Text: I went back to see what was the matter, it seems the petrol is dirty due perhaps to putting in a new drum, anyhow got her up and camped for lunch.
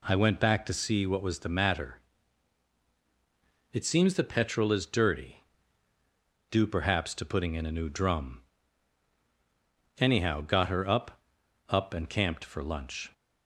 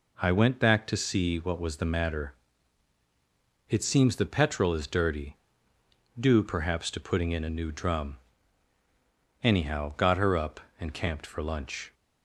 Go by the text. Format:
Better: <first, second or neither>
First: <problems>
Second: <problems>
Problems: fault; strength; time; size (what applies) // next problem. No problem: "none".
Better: second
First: pauses between "dirty" and "due"; at 5.4 s; 1.0 s long // says "up" twice; at 11.6 s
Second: pauses between "dirty" and "due"; noticeable; at 5.3 s; 0.80 s long